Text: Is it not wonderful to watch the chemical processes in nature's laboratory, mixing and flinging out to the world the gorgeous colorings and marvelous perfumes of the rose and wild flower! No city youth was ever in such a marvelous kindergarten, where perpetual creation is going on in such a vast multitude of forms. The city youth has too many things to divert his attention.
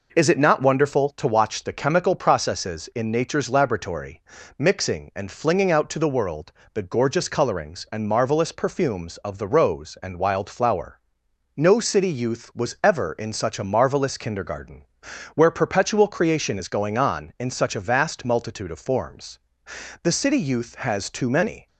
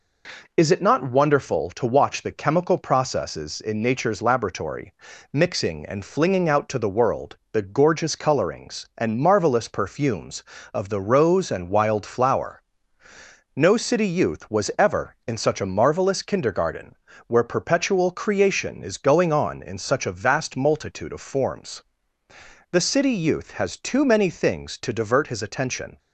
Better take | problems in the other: second | pauses between "world" and "the"; slight; at 6.5 s; 0.22 s long; slight in the second // stops before "things to divert his attention"; at 21.6 s

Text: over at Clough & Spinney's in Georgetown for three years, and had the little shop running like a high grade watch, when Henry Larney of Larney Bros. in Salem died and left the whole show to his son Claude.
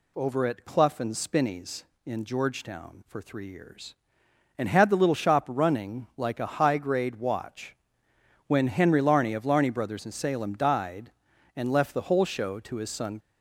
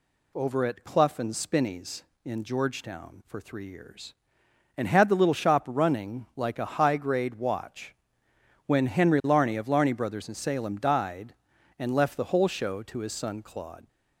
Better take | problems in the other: second | stops before "Claude"; at 13.1 s

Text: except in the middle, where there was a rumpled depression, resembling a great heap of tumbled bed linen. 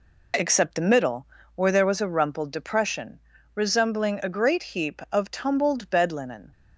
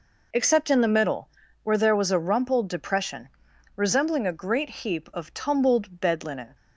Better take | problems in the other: second | skips "in"; at 0.7 s

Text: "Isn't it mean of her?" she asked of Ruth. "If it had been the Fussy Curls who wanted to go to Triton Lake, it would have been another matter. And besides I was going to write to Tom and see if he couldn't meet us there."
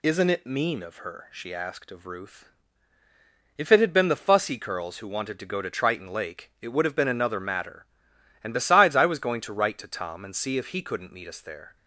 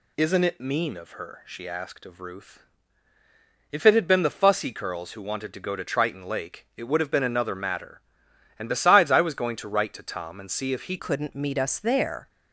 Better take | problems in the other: first | changes voice at "couldn't"; from 10.9 s on; 1.3 s long

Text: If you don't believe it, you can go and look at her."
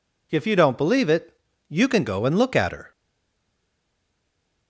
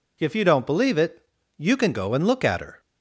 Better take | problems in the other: second | stays silent after the last word; noticeable; from 2.9 s on; 1.7 s long

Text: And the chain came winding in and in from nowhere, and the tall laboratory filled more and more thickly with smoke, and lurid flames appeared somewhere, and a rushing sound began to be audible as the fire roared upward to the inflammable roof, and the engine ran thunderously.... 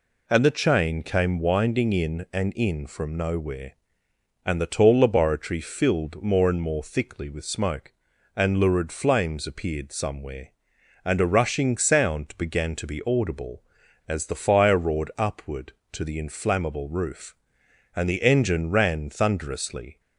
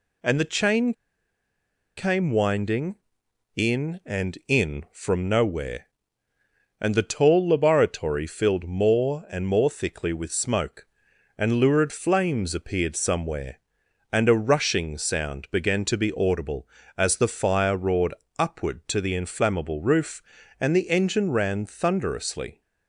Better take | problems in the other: first | pauses between "chain" and "came"; at 0.9 s; 1.0 s long // pauses between "roared" and "upward"; slight; at 18.1 s; 0.24 s long

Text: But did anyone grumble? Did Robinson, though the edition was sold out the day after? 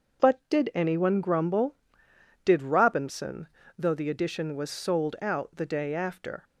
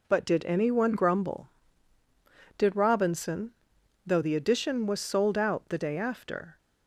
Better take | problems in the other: neither | none

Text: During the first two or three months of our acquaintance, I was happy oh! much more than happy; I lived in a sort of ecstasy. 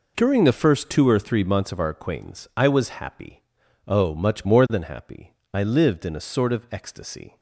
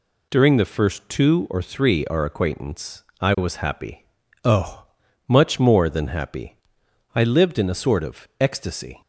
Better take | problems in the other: first | skips "months of"; at 2.0 s // pauses between "happy" and "oh"; at 4.0 s; 0.40 s long; also in the first

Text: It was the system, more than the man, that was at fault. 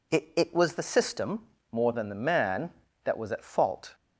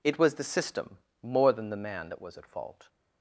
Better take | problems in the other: second | says "It" twice; at 0.3 s

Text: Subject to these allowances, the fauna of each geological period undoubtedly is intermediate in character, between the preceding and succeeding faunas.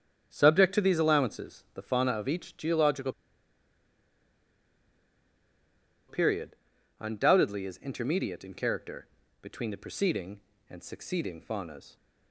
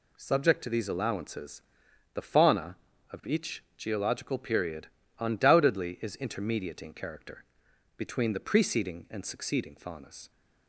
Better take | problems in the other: second | starts louder than the rest; strong; until 1.3 s; 8 dB // pauses between "geological" and "period"; strong; at 3.1 s; 2.9 s long // pauses between "period" and "undoubtedly"; noticeable; at 6.5 s; 0.46 s long; slight in the second

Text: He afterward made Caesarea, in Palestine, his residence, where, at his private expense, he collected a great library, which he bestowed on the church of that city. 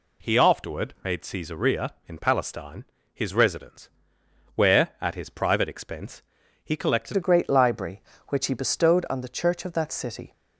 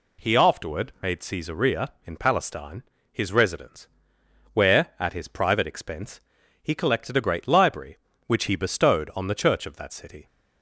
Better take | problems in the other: second | changes voice at "a"; from 7.1 s on; 3.2 s long

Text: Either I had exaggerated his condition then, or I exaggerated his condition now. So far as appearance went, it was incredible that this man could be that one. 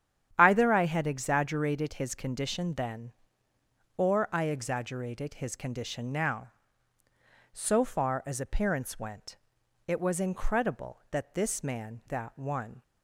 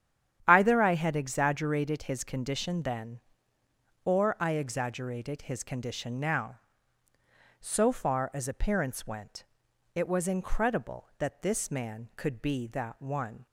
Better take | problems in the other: second | starts louder than the rest; strong; until 1.3 s; 9.5 dB; strong in the second // skips "could be"; at 12.0 s

